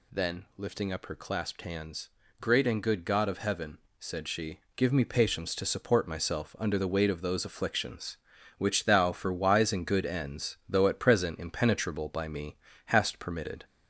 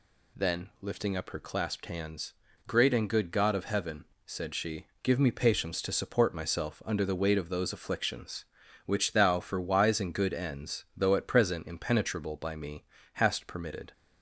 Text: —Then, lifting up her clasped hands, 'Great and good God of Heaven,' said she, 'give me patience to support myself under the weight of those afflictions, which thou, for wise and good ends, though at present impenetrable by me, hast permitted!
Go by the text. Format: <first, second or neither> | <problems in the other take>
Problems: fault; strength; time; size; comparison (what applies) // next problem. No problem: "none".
second | gets louder; slight; throughout; 2.5 dB